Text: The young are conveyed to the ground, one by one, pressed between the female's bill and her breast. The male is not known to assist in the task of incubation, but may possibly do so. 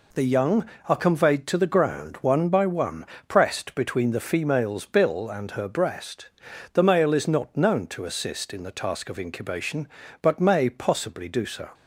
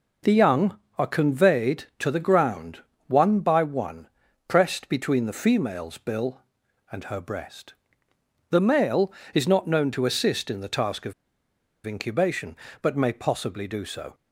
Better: first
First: none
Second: pauses between "of" and "incubation"; noticeable; at 11.1 s; 0.71 s long

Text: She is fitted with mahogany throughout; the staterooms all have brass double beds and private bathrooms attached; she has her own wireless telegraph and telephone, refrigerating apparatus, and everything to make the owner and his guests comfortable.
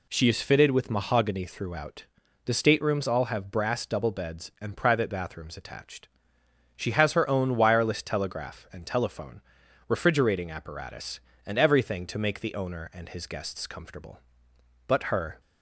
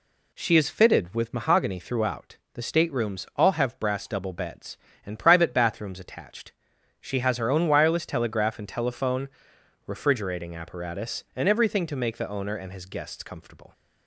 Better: second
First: goes on to say "But her"; from 14.8 s on; 0.54 s long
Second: none

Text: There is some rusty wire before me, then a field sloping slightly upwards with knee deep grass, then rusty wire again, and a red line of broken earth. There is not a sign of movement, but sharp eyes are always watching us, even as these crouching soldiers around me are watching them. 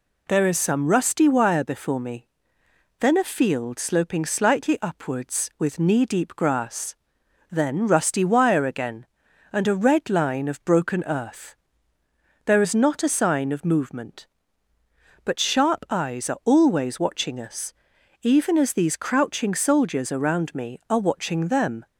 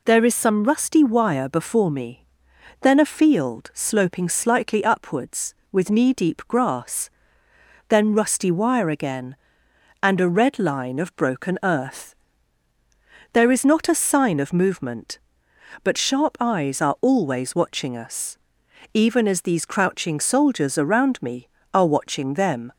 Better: neither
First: none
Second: none

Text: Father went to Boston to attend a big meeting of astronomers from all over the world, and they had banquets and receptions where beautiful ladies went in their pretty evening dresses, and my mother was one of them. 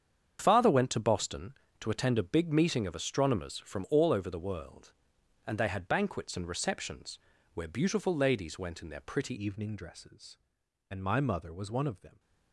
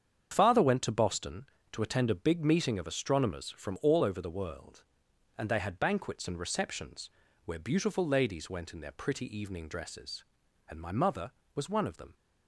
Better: second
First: starts louder than the rest; strong; until 1.4 s; 8 dB // pauses between "receptions" and "where"; slight; at 7.1 s; 0.34 s long // changes voice at "evening"; from 9.3 s on; 2.8 s long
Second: starts louder than the rest; strong; until 1.3 s; 8 dB // pauses between "receptions" and "where"; slight; at 7.0 s; 0.34 s long

